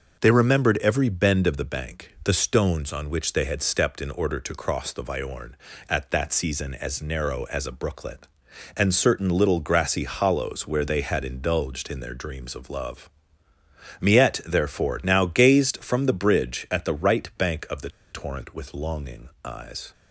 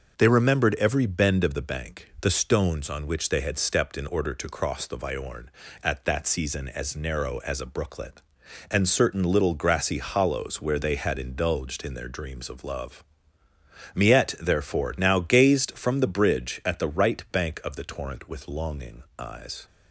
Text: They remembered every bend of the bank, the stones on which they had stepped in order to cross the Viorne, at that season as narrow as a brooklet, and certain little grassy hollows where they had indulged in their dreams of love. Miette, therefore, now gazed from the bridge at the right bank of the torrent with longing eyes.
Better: second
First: pauses between "the" and "torrent"; slight; at 17.8 s; 0.21 s long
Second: none

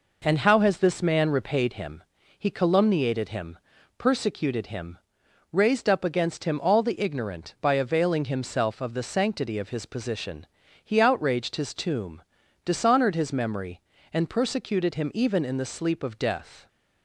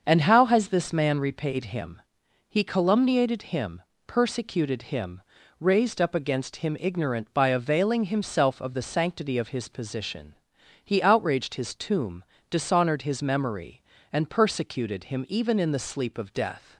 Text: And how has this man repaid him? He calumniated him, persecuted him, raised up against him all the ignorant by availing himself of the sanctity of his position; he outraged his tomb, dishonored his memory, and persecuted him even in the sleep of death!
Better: first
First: none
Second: starts louder than the rest; until 1.0 s; 6.5 dB // skips "all the"; at 6.7 s

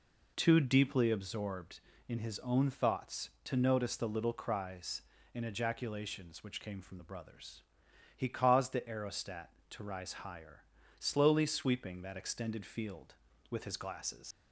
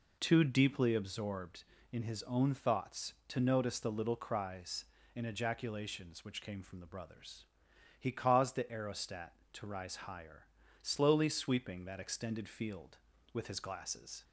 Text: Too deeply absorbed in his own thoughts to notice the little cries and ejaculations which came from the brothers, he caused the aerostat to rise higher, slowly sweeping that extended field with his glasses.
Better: second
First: leaves "glasses" unfinished; at 14.3 s; 95 ms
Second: none

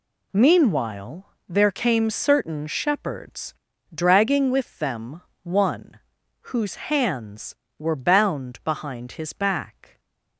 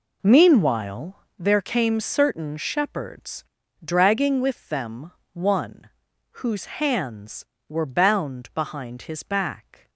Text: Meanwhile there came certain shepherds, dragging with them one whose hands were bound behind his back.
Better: first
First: pauses between "Meanwhile" and "there"; slight; at 1.2 s; 0.22 s long // pauses between "them" and "one"; slight; at 5.2 s; 0.20 s long // pauses between "one" and "whose"; noticeable; at 5.9 s; 0.56 s long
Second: starts louder than the rest; until 1.5 s; 3.5 dB // pauses between "Meanwhile" and "there"; slight; at 1.1 s; 0.22 s long // pauses between "them" and "one"; slight; at 5.1 s; 0.20 s long // pauses between "one" and "whose"; noticeable; at 5.8 s; 0.56 s long

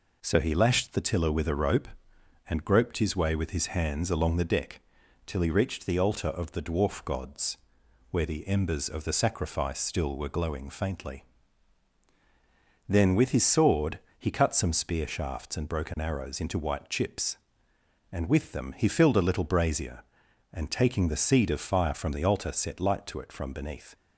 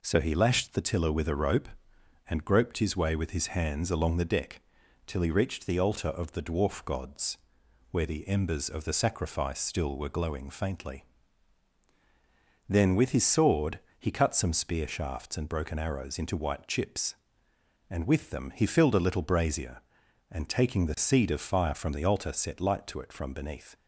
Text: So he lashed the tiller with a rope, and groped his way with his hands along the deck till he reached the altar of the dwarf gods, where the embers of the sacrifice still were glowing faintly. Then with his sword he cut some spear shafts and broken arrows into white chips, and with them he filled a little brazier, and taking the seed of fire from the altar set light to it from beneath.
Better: neither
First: pauses between "deck" and "till"; at 4.8 s; 0.44 s long // pauses between "sword" and "he"; slight; at 14.0 s; 0.18 s long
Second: pauses between "deck" and "till"; at 4.6 s; 0.44 s long // pauses between "sword" and "he"; slight; at 13.8 s; 0.18 s long

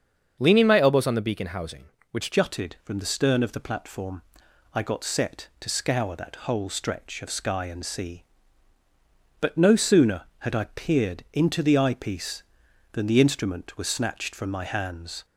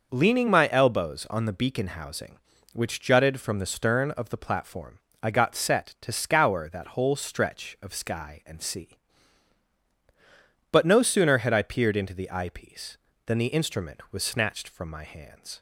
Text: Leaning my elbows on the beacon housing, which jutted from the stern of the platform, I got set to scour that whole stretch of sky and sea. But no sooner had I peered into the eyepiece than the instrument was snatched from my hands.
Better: second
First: starts louder than the rest; until 1.4 s; 7 dB // changes voice at "jutted"; from 2.3 s on; 12.9 s long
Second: starts louder than the rest; noticeable; until 1.1 s; 6 dB

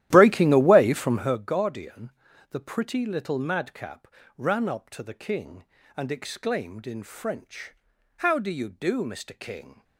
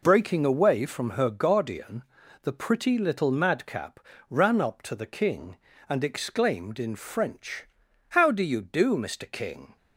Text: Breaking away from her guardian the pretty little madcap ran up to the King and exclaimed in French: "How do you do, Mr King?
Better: second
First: starts louder than the rest; strong; until 1.4 s; 13 dB // pauses between "guardian" and "the"; at 2.1 s; 0.38 s long // pauses between "madcap" and "ran"; slight; at 4.0 s; 0.28 s long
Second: pauses between "guardian" and "the"; at 2.0 s; 0.38 s long // pauses between "madcap" and "ran"; slight; at 3.9 s; 0.28 s long

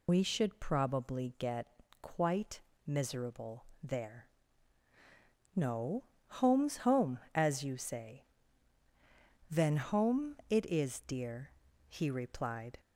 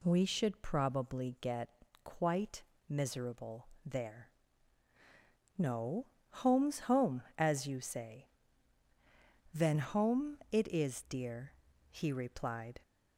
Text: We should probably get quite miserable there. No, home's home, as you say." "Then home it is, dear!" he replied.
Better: second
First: loses the start of "We"; at 0.0 s; 95 ms // pauses between "get" and "quite"; slight; at 1.6 s; 0.34 s long // pauses between "quite" and "miserable"; slight; at 2.5 s; 0.26 s long // pauses between "miserable" and "there"; slight; at 3.6 s; 0.18 s long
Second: pauses between "get" and "quite"; slight; at 1.6 s; 0.34 s long // pauses between "quite" and "miserable"; slight; at 2.6 s; 0.26 s long // pauses between "miserable" and "there"; slight; at 3.6 s; 0.18 s long

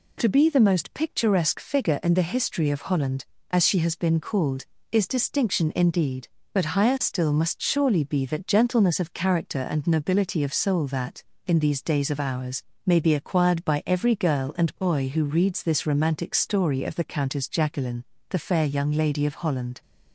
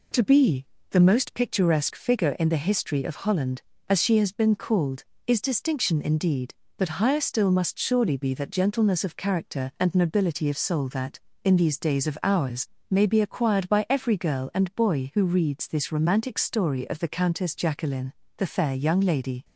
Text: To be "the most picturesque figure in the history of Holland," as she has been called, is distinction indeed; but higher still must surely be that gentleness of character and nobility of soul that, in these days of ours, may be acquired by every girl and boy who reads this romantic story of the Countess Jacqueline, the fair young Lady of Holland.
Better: first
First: none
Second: pauses between "be" and "the"; slight; at 0.6 s; 0.24 s long // stops before "of Holland"; at 19.4 s

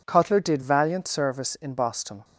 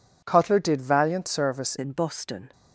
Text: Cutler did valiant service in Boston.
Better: first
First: none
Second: changes voice at "in"; from 1.7 s on; 0.8 s long

